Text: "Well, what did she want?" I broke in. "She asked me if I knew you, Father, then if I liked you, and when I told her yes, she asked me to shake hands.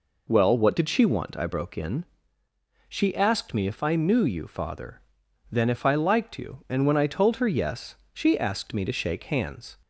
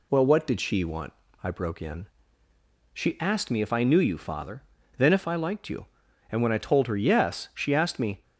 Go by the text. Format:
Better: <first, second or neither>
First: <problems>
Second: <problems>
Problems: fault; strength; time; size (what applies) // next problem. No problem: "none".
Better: first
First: none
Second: stops before "to shake hands"; at 8.2 s